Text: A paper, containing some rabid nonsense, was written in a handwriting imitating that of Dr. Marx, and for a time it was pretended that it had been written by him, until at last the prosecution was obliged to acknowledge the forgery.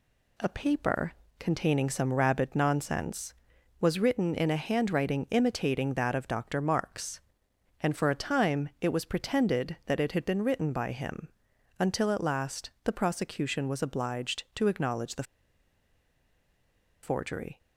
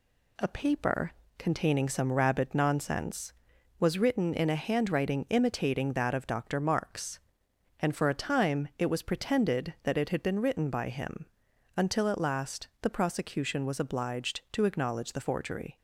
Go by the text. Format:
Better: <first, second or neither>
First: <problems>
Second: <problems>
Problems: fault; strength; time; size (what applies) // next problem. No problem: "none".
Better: second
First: pauses between "last" and "the"; slight; at 12.6 s; 0.16 s long // pauses between "the" and "forgery"; strong; at 15.2 s; 1.8 s long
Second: pauses between "last" and "the"; slight; at 12.6 s; 0.16 s long